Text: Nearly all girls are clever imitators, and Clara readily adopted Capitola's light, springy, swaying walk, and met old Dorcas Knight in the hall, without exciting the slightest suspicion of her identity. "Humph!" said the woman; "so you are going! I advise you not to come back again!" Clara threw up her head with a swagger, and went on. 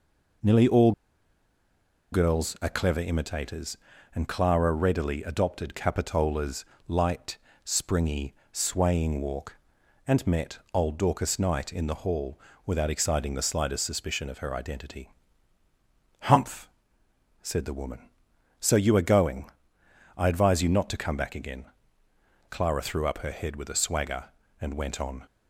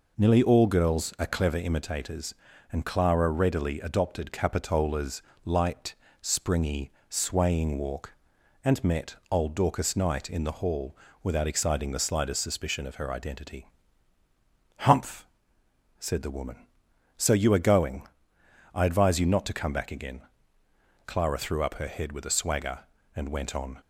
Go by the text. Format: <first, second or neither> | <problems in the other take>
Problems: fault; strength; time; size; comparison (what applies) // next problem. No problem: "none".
second | pauses between "all" and "girls"; at 0.9 s; 1.2 s long // pauses between "Capitola's" and "light"; slight; at 6.6 s; 0.22 s long; slight in the second